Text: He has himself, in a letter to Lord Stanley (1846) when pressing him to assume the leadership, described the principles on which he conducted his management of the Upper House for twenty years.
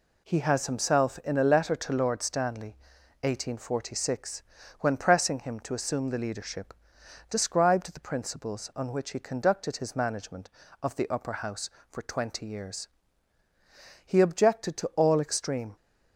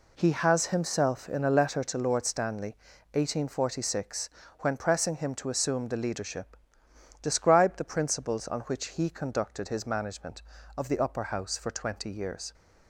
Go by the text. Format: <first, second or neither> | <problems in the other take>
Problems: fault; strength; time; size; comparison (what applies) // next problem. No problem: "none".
second | goes on to say "He objected to all extreme"; strong; from 14.0 s on; 1.7 s long